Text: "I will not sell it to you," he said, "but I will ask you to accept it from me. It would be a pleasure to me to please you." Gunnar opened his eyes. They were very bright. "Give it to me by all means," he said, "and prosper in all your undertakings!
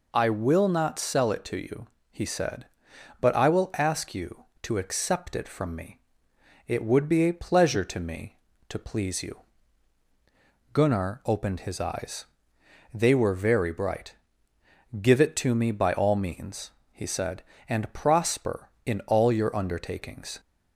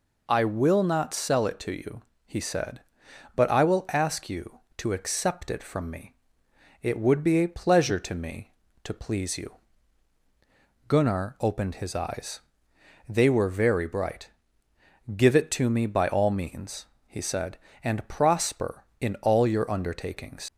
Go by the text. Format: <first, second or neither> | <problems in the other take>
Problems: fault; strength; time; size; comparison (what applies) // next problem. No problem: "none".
first | leaves "undertakings" unfinished; at 20.4 s; 65 ms